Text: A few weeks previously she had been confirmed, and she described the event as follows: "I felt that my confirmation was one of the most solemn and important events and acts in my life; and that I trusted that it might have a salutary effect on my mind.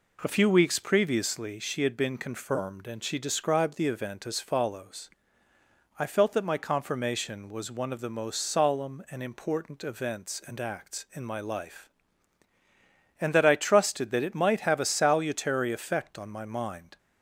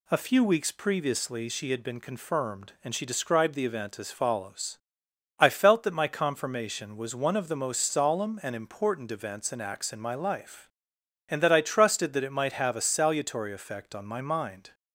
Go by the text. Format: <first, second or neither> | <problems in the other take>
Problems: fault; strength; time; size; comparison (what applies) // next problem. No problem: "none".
neither | none